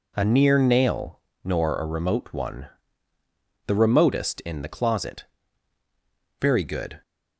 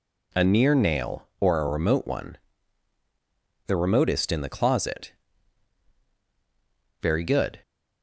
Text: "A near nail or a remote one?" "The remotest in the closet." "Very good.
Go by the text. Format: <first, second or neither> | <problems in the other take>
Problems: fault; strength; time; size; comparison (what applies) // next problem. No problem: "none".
second | says "nor" for "or"; at 1.4 s